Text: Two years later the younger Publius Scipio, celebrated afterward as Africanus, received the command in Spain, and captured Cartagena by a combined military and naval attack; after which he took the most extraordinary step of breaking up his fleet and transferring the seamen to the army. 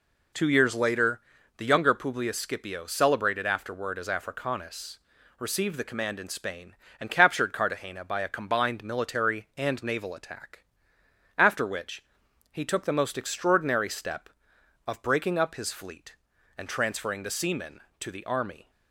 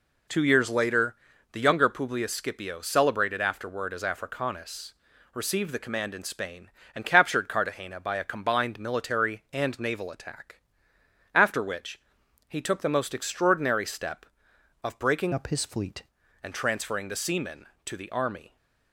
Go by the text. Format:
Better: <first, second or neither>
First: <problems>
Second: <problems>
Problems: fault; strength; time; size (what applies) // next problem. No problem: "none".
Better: first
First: pauses between "later" and "the"; at 1.1 s; 0.38 s long // pauses between "which" and "he"; noticeable; at 12.0 s; 0.50 s long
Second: pauses between "later" and "the"; at 1.1 s; 0.38 s long // pauses between "which" and "he"; noticeable; at 11.9 s; 0.50 s long // changes voice from "up" to "fleet"; from 15.3 to 16.0 s; 0.7 s long